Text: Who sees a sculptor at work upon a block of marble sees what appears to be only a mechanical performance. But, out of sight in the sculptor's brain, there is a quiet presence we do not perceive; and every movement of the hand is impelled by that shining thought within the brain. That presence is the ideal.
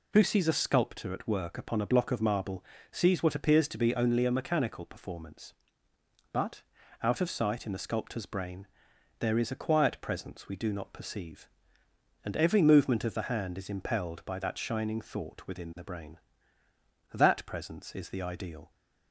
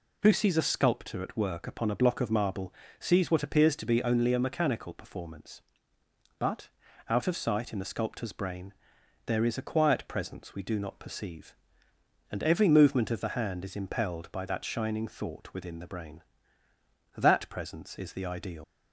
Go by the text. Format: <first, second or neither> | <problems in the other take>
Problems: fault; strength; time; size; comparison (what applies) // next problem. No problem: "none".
first | pauses between "marble" and "sees"; slight; at 2.7 s; 0.26 s long; slight in the first // leaves "ideal" unfinished; at 18.6 s; 95 ms